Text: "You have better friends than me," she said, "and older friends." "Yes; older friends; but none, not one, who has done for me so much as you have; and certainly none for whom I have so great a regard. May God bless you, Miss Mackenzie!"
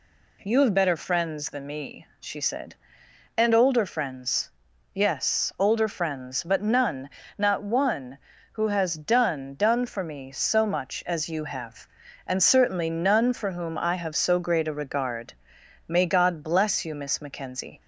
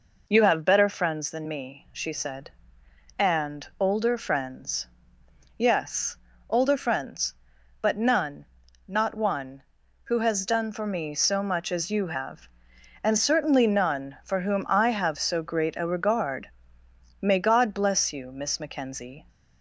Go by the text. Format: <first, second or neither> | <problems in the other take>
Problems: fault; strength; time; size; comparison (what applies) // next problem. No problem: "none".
second | says "done" twice; at 9.5 s